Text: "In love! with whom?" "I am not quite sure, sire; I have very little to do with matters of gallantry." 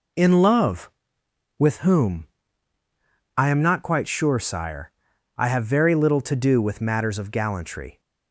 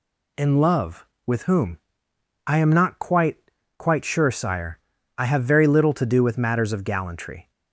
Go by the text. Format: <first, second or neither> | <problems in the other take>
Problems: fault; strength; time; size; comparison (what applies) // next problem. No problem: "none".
first | says "quite" twice; at 3.7 s